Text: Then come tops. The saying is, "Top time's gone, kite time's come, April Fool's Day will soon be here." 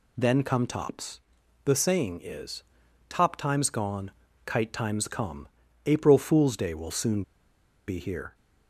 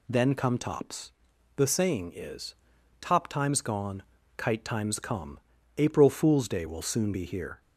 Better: second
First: pauses between "soon" and "be"; noticeable; at 7.2 s; 0.64 s long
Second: none

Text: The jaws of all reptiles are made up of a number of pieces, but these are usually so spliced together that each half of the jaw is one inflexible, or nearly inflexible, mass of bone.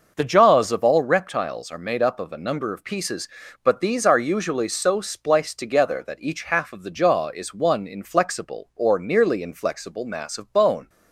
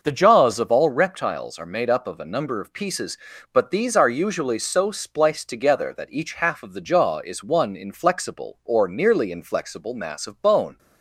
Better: neither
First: starts louder than the rest; noticeable; until 1.1 s; 6 dB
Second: starts louder than the rest; noticeable; until 1.0 s; 6 dB

